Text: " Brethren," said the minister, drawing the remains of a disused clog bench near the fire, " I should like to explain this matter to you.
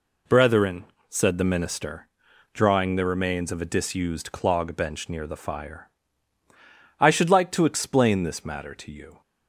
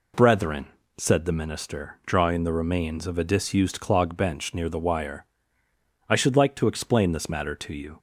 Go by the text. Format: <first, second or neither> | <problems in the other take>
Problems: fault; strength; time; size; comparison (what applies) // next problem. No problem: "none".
first | says "wire" for "fire"; at 4.7 s